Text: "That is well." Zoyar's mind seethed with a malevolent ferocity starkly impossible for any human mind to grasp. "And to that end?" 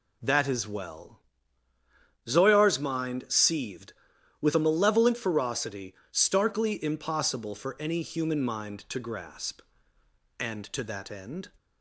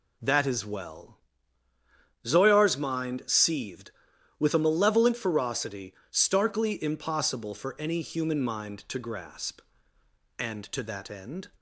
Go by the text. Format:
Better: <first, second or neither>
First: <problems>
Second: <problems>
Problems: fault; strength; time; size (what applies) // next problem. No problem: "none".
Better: neither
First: pauses between "ferocity" and "starkly"; slight; at 5.9 s; 0.18 s long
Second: pauses between "ferocity" and "starkly"; slight; at 5.9 s; 0.18 s long